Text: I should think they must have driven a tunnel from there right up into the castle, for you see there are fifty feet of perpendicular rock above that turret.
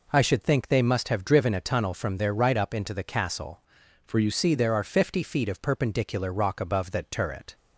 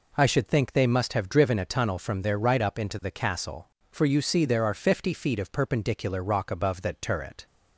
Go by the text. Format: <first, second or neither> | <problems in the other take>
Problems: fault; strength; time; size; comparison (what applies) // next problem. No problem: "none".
second | changes voice from "for" to "you"; from 4.0 to 4.2 s; 0.2 s long